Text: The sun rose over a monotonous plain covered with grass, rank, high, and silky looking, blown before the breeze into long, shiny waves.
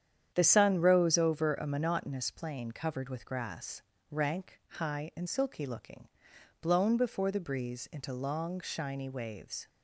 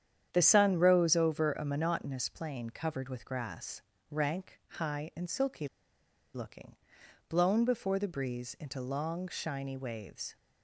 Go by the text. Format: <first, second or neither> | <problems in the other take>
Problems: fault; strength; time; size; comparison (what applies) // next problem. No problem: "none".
first | starts louder than the rest; strong; until 1.3 s; 9 dB; strong in the first // pauses between "silky" and "looking"; noticeable; at 5.6 s; 0.68 s long